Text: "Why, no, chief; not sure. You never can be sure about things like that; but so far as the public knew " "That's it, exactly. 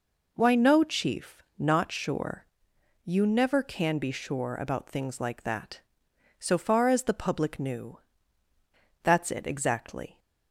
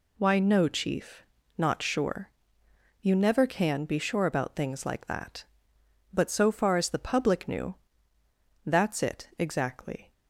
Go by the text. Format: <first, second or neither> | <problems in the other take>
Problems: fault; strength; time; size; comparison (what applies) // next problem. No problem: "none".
second | skips "but"; at 6.1 s